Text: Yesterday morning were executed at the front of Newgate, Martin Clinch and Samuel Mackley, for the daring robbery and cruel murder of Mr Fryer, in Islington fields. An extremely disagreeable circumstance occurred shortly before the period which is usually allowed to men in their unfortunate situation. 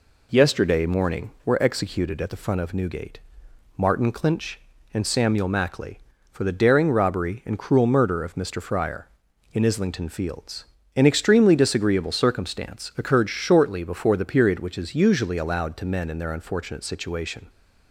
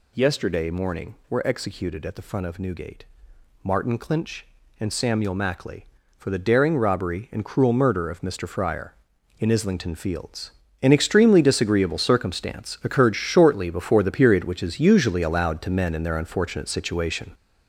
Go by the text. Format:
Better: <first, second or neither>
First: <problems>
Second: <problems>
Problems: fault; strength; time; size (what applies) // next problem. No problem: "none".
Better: first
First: none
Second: gets louder; throughout; 6.5 dB